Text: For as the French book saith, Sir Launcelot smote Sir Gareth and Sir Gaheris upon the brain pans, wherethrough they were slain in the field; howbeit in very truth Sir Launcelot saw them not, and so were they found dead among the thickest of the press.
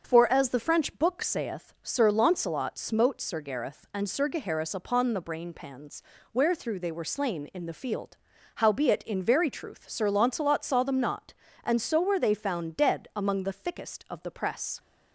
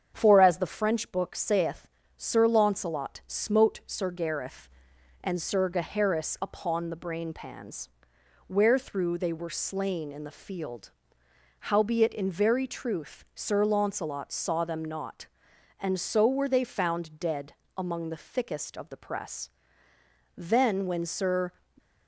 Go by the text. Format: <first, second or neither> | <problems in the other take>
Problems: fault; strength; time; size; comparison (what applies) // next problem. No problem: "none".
first | starts louder than the rest; strong; until 1.1 s; 7.5 dB; also in the first // pauses between "dead" and "among"; slight; at 17.5 s; 0.22 s long // goes on to say "Then when Sir"; noticeable; from 20.3 s on; 1.1 s long